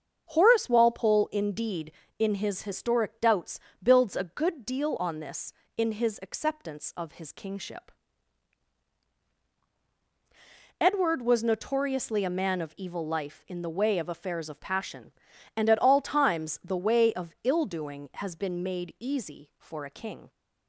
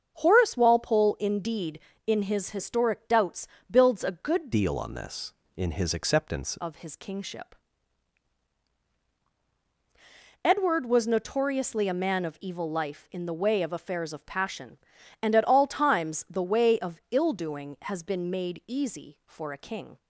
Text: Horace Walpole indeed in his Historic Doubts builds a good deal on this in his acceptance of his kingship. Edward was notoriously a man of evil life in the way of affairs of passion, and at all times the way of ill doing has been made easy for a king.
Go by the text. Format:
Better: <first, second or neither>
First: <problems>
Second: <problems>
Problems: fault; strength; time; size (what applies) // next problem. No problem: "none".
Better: first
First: starts louder than the rest; until 1.3 s; 7 dB // pauses between "Doubts" and "builds"; slight; at 3.5 s; 0.22 s long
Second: starts louder than the rest; until 1.2 s; 7 dB // pauses between "Doubts" and "builds"; slight; at 3.4 s; 0.22 s long // changes voice from "deal" to "acceptance"; from 4.5 to 6.5 s; 2.0 s long